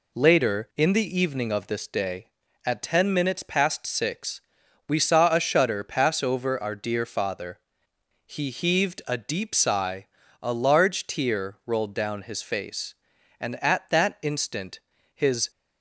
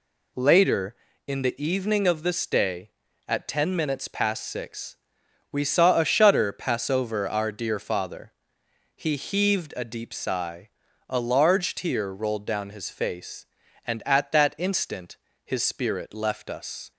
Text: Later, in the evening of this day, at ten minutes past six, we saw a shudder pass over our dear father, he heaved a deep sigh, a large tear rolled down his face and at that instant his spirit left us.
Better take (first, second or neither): second